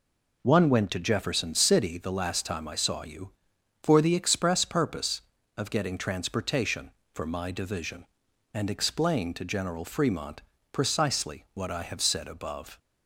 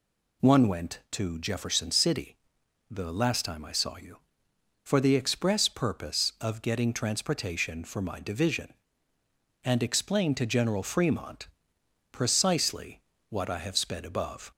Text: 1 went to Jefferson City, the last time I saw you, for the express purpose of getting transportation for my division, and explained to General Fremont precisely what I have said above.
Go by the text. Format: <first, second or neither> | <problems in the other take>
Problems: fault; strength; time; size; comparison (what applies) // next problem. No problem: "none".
first | pauses between "Fremont" and "precisely"; noticeable; at 11.4 s; 0.64 s long; slight in the first // pauses between "precisely" and "what"; slight; at 13.0 s; 0.28 s long // says "sped" for "said"; at 13.7 s